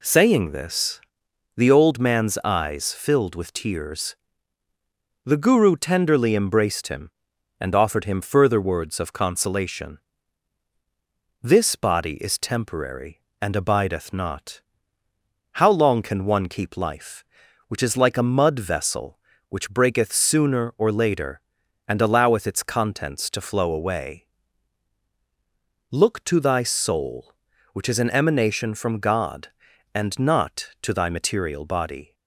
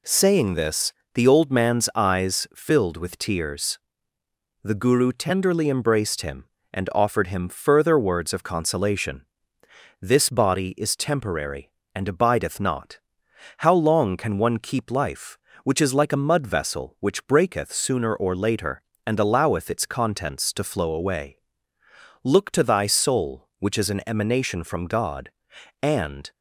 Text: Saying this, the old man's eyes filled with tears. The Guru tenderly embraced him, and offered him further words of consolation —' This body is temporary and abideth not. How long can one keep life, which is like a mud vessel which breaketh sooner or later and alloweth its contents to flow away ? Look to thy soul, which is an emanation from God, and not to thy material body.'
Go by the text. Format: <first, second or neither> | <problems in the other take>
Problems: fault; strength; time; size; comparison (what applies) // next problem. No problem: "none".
first | stops before "not to thy material body"; at 26.3 s